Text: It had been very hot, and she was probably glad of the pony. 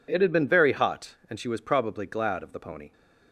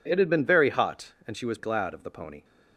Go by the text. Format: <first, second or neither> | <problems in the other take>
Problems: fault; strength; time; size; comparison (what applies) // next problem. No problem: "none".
first | skips "probably"; at 1.5 s